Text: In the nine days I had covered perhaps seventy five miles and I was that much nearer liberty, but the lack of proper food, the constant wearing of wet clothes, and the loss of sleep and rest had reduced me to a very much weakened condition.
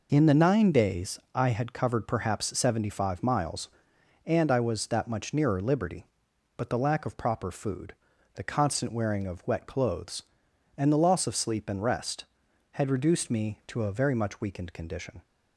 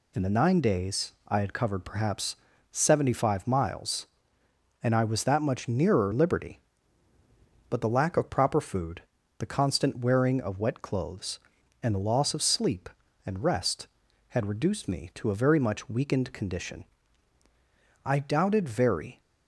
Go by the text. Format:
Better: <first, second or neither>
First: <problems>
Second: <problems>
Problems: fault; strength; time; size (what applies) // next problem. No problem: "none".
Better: first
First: none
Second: pauses between "perhaps" and "seventy"; slight; at 2.3 s; 0.36 s long // goes on to say "I doubted very"; noticeable; from 18.0 s on; 1.1 s long